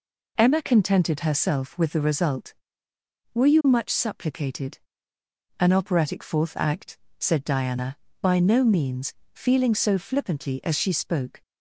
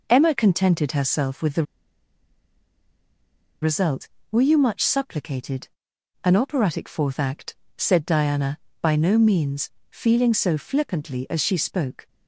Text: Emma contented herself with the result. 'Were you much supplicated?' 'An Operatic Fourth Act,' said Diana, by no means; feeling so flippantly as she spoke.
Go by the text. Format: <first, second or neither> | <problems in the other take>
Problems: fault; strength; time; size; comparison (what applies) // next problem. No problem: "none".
first | pauses between "the" and "result"; strong; at 1.6 s; 1.9 s long